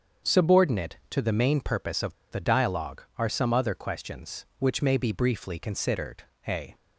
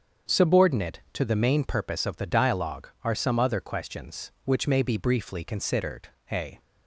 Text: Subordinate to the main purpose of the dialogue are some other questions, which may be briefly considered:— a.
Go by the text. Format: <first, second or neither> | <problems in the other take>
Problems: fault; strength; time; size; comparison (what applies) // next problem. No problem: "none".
second | starts louder than the rest; until 1.3 s; 7 dB; also in the second // pauses between "of" and "the"; slight; at 2.1 s; 0.17 s long